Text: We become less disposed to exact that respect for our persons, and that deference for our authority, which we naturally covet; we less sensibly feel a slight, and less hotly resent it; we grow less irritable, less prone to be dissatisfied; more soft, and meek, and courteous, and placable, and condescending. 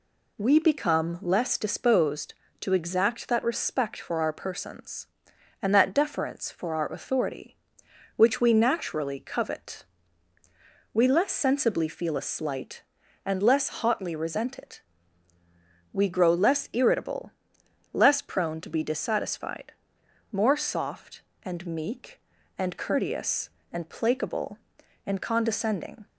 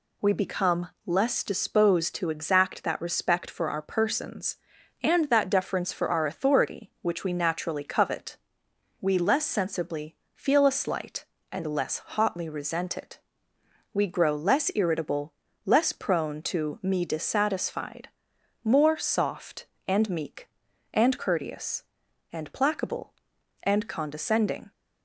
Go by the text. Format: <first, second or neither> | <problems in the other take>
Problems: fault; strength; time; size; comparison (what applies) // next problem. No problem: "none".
first | pauses between "become" and "less"; slight; at 0.8 s; 0.18 s long // pauses between "sensibly" and "feel"; slight; at 10.1 s; 0.18 s long // says "me" for "be"; at 16.8 s